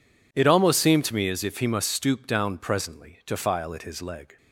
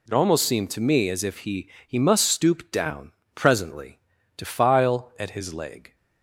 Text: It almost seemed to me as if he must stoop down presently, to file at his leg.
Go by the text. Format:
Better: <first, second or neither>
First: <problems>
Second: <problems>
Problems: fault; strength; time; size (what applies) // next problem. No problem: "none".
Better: first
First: none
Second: says "he" twice; at 1.8 s // pauses between "down" and "presently"; slight; at 3.1 s; 0.24 s long